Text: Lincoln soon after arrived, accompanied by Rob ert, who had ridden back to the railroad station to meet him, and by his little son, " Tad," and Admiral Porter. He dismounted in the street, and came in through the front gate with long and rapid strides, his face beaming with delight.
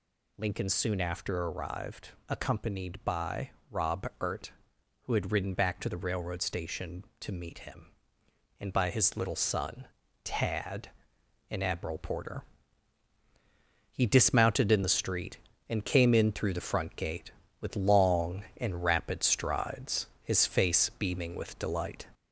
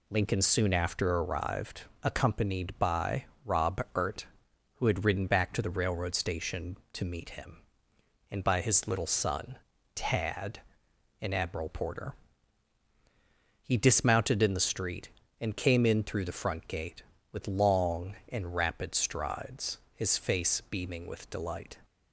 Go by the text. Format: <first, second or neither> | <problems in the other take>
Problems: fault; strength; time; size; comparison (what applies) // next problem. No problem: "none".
second | gets louder; slight; throughout; 3.5 dB // pauses between "by" and "Rob"; slight; at 3.4 s; 0.20 s long; slight in the second